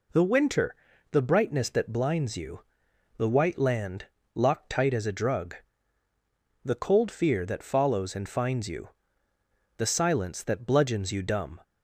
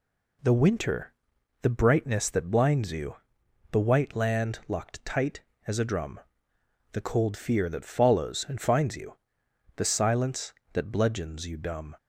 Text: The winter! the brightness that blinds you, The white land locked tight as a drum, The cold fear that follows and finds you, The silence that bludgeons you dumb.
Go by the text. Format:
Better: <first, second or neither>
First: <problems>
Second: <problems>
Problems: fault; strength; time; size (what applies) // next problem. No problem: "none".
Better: second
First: pauses between "land" and "locked"; slight; at 4.0 s; 0.28 s long // says "drug" for "drum"; at 5.1 s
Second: none